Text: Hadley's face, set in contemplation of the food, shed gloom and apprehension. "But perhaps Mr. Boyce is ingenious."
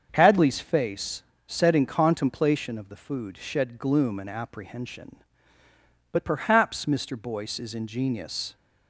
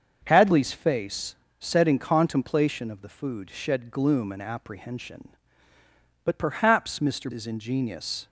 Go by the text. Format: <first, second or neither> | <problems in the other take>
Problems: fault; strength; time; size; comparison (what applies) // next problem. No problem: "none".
first | starts louder than the rest; until 1.2 s; 6.5 dB; also in the first // skips "Boyce"; at 7.3 s